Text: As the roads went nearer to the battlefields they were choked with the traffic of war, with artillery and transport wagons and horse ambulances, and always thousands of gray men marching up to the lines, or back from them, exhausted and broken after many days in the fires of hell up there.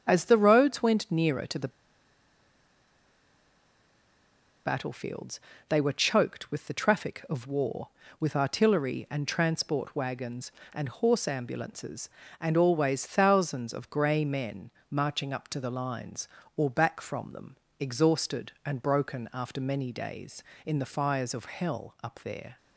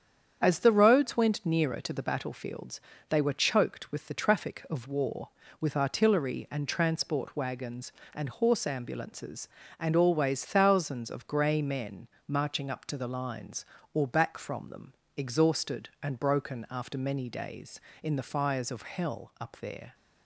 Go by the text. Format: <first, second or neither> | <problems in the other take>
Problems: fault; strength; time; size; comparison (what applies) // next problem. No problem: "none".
second | starts louder than the rest; strong; until 1.0 s; 8.5 dB; strong in the second // pauses between "the" and "battlefields"; strong; at 1.6 s; 2.9 s long // pauses between "battlefields" and "they"; slight; at 5.3 s; 0.30 s long; slight in the second // pauses between "men" and "marching"; slight; at 14.7 s; 0.20 s long; slight in the second